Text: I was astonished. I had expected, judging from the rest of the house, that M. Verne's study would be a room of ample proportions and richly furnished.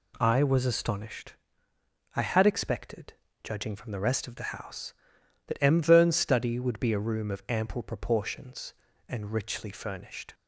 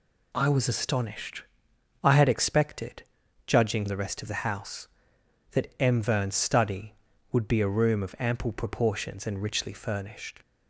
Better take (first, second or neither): first